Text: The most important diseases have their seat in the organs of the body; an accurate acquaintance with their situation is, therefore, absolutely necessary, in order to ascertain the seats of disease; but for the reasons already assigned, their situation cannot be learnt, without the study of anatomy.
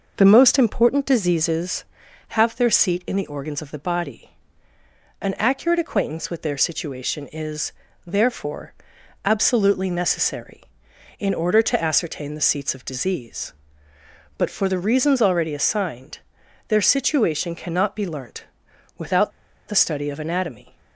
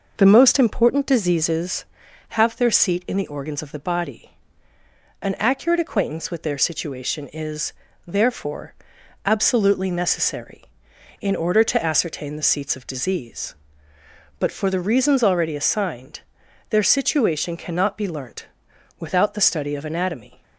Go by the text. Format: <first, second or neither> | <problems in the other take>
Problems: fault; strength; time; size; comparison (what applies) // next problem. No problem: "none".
second | pauses between "without" and "the"; at 19.3 s; 0.37 s long